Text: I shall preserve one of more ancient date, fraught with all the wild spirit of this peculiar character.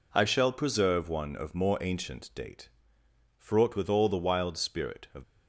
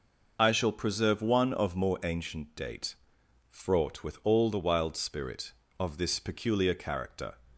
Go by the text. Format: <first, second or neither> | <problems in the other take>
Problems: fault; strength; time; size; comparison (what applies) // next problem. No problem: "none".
second | stops before "this peculiar character"; at 5.2 s